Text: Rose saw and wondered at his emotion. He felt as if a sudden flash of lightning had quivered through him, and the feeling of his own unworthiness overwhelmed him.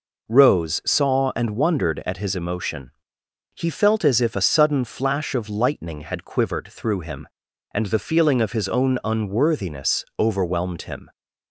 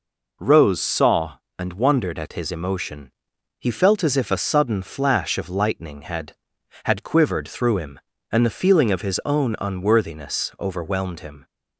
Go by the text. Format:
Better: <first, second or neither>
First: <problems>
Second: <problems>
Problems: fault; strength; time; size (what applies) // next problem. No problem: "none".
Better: first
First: none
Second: says "had" twice; at 6.8 s